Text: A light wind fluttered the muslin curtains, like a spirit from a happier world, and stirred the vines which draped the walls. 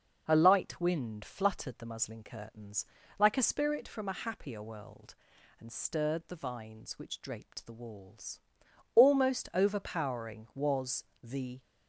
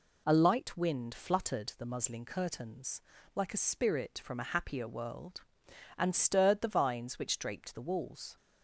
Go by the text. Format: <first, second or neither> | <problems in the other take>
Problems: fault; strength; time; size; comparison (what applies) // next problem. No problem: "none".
second | goes on to say "Almost overpowering was the"; strong; from 8.9 s on; 2.6 s long